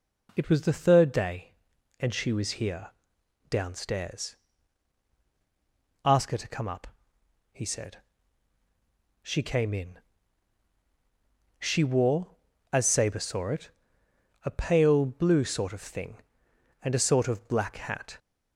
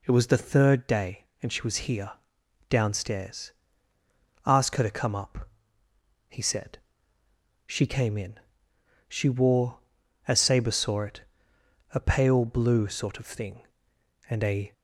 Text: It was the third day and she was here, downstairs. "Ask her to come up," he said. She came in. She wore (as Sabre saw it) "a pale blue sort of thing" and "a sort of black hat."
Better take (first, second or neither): first